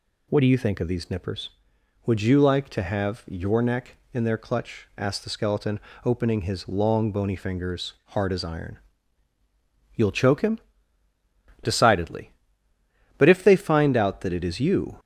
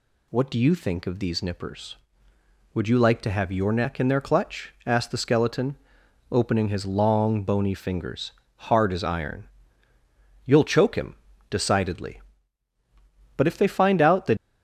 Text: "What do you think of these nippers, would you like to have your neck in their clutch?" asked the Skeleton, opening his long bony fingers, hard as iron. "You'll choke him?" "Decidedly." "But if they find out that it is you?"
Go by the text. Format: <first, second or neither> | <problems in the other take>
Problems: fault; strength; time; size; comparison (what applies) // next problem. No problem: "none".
first | stops before "it is you"; at 14.3 s